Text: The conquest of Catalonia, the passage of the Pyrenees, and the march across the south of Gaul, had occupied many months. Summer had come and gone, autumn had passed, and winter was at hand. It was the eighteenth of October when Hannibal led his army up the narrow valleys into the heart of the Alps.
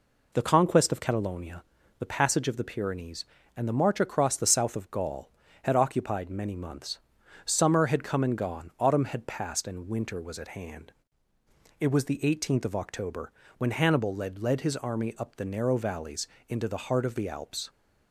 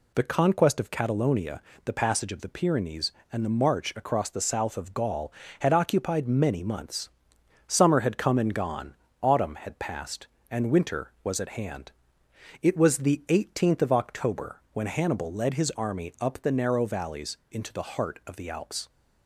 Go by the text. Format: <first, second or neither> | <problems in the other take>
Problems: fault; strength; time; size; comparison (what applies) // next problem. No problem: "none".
second | pauses between "October" and "when"; slight; at 13.3 s; 0.28 s long // says "led" twice; at 14.3 s // pauses between "valleys" and "into"; slight; at 16.2 s; 0.22 s long